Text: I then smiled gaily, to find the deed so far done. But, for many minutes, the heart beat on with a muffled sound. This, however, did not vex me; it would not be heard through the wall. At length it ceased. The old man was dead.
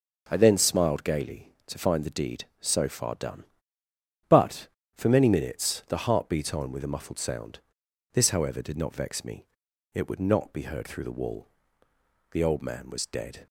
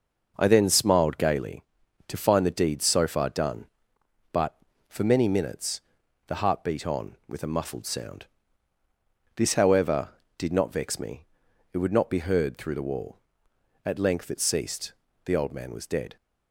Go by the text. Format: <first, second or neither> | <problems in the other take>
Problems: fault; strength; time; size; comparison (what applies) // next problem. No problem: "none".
second | skips "At length it ceased"; at 11.8 s